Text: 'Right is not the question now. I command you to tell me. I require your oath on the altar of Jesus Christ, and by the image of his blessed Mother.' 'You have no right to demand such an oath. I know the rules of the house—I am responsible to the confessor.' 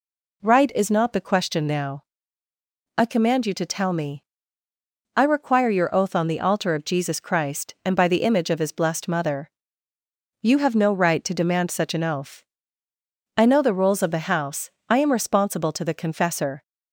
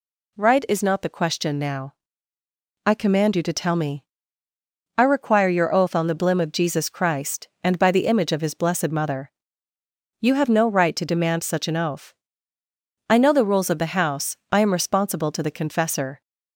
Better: first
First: none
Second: says "blim" for "altar"; at 6.1 s

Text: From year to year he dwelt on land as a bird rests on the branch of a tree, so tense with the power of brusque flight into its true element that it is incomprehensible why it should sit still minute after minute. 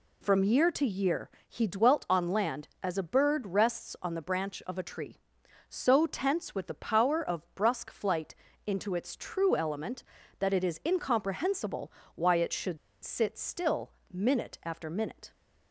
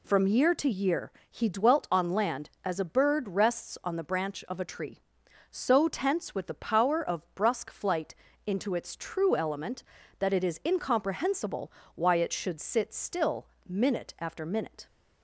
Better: second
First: pauses between "year" and "he"; slight; at 1.3 s; 0.18 s long // pauses between "flight" and "into"; slight; at 8.3 s; 0.28 s long // pauses between "incomprehensible" and "why"; slight; at 11.9 s; 0.24 s long // pauses between "should" and "sit"; slight; at 12.7 s; 0.26 s long // pauses between "still" and "minute"; slight; at 13.9 s; 0.22 s long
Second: pauses between "year" and "he"; slight; at 1.1 s; 0.18 s long // pauses between "flight" and "into"; slight; at 8.1 s; 0.28 s long // pauses between "incomprehensible" and "why"; slight; at 11.6 s; 0.24 s long // pauses between "still" and "minute"; slight; at 13.4 s; 0.22 s long

